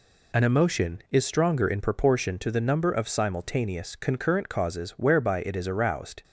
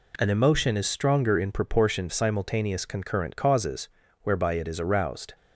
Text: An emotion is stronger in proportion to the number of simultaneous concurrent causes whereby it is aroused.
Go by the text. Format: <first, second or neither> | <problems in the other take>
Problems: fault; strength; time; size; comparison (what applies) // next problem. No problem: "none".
first | skips "to the number of"; at 2.0 s // pauses between "causes" and "whereby"; slight; at 3.8 s; 0.34 s long